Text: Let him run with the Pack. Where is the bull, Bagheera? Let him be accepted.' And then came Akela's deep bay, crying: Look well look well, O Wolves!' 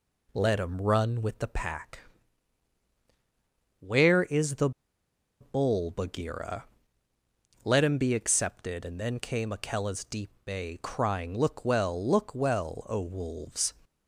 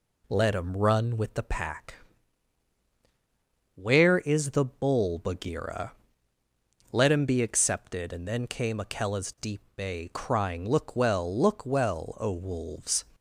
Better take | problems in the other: second | pauses between "the" and "bull"; noticeable; at 4.6 s; 0.70 s long

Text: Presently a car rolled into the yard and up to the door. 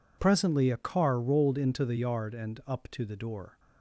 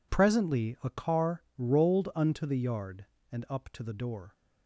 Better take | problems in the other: first | says "unto" for "into"; at 2.1 s

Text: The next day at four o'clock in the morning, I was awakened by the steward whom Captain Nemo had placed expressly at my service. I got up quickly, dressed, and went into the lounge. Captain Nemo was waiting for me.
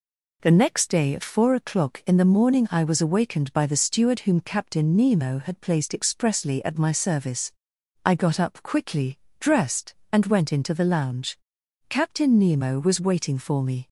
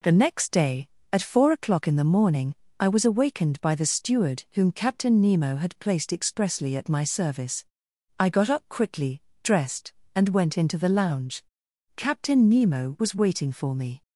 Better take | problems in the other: neither | none

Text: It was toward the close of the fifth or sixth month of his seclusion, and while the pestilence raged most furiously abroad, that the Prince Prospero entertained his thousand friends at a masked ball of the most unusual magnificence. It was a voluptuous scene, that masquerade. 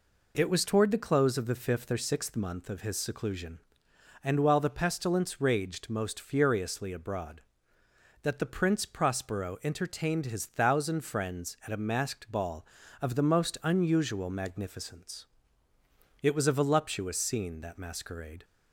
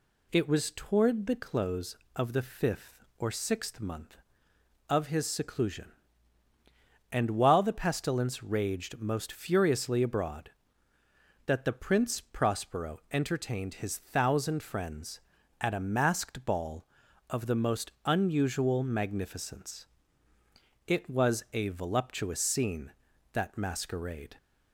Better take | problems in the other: neither | none

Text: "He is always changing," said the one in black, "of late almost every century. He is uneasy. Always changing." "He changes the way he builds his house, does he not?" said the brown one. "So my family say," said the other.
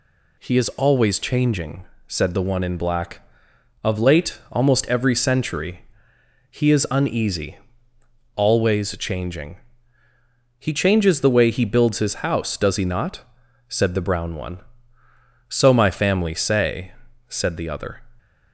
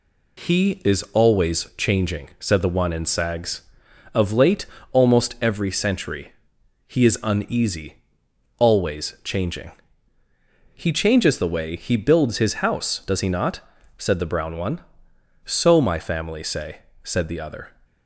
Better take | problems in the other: first | says "sags" for "black"; at 3.0 s // pauses between "late" and "almost"; slight; at 4.6 s; 0.26 s long

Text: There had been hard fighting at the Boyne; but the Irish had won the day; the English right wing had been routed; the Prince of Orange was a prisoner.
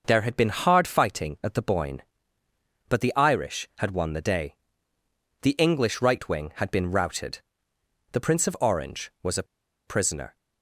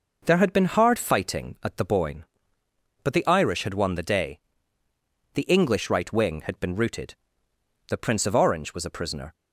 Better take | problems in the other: second | pauses between "a" and "prisoner"; at 9.4 s; 0.43 s long

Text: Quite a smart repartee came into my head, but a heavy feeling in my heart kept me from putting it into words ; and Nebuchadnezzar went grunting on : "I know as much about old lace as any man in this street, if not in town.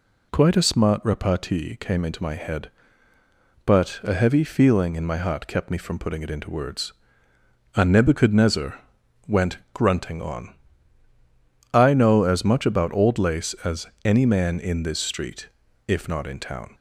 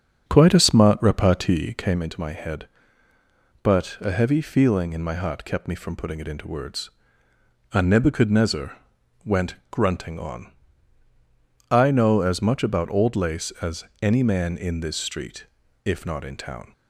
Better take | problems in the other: first | starts louder than the rest; strong; until 2.0 s; 7 dB // pauses between "Nebuchadnezzar" and "went"; noticeable; at 8.7 s; 0.48 s long; noticeable in the first // pauses between "went" and "grunting"; slight; at 9.5 s; 0.16 s long; slight in the first // pauses between "as" and "any"; slight; at 13.8 s; 0.18 s long; slight in the first

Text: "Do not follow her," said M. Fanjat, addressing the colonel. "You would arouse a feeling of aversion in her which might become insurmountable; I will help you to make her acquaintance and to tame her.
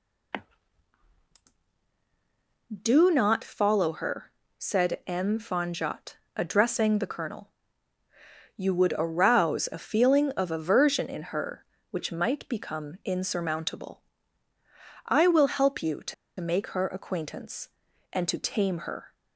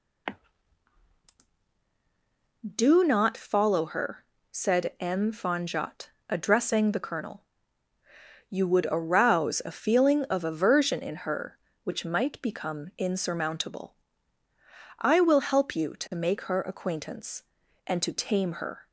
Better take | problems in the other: second | pauses between "to" and "make"; slight; at 16.1 s; 0.27 s long

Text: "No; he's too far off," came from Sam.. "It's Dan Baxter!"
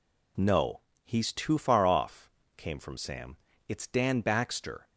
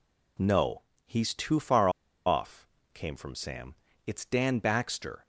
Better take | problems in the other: first | pauses between "far" and "off"; at 1.8 s; 0.36 s long

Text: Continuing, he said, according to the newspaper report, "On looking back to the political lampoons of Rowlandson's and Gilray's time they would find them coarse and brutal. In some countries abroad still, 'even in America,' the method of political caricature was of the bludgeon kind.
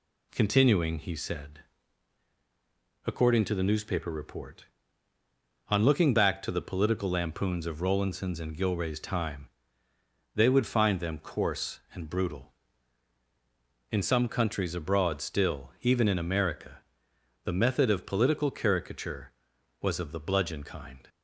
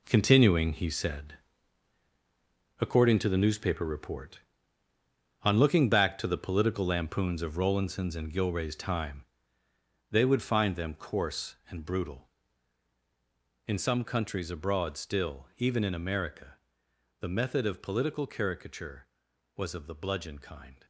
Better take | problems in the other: first | gets quieter; strong; throughout; 9.5 dB // pauses between "time" and "they"; noticeable; at 9.2 s; 0.86 s long; noticeable in the first

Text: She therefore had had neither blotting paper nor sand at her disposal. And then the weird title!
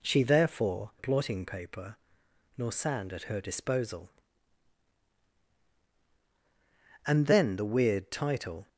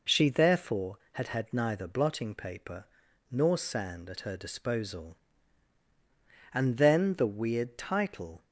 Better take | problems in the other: second | skips "had had neither"; at 0.9 s // pauses between "paper" and "nor"; noticeable; at 1.9 s; 0.60 s long; also in the second

